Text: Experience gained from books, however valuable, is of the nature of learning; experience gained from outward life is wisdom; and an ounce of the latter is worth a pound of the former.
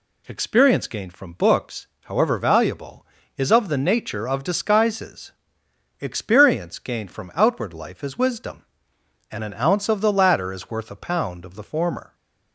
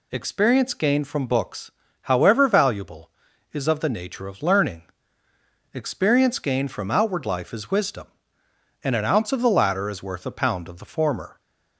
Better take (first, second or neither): second